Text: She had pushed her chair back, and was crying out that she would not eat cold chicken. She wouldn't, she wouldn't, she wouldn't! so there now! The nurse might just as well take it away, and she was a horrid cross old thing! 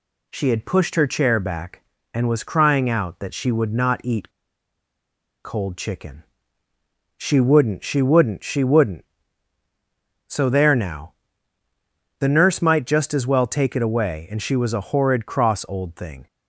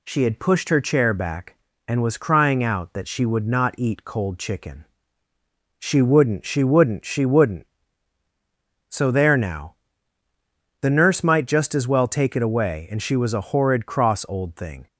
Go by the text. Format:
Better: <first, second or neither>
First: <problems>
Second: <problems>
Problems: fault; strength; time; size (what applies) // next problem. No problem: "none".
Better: second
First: pauses between "eat" and "cold"; at 4.3 s; 1.1 s long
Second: none